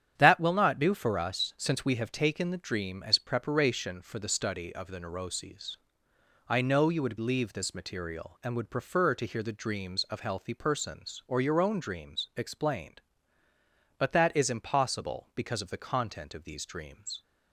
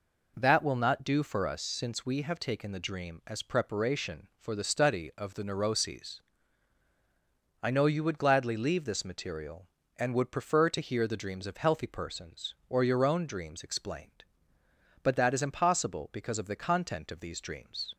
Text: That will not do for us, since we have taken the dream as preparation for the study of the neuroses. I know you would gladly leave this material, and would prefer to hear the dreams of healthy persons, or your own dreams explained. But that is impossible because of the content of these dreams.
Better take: second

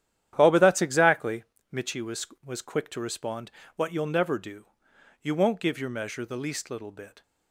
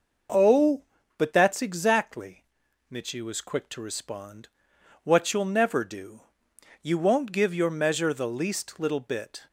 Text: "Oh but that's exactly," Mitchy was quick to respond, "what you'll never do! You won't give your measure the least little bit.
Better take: second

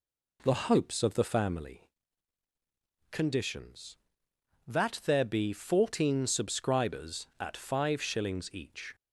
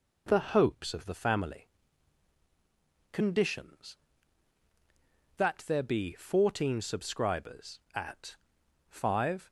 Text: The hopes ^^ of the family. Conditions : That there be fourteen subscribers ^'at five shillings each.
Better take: first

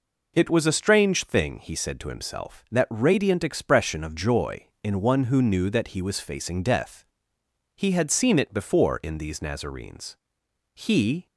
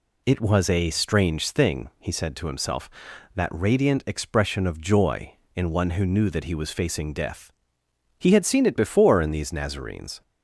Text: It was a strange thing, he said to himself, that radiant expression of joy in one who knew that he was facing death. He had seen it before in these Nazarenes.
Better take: second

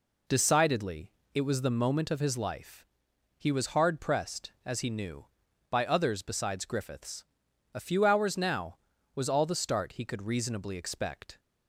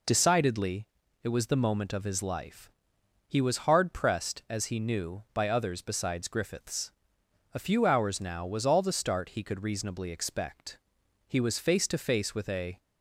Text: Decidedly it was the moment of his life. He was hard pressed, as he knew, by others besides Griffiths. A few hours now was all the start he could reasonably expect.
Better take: first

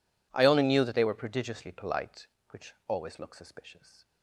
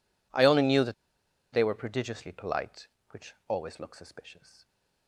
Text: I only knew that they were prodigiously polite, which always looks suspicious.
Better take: first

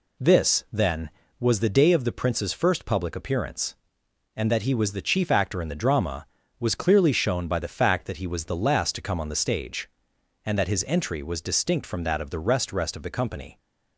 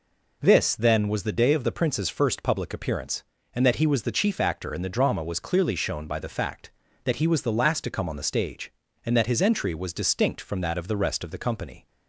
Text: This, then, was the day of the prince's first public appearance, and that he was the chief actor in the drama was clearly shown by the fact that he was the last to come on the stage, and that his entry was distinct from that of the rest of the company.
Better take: second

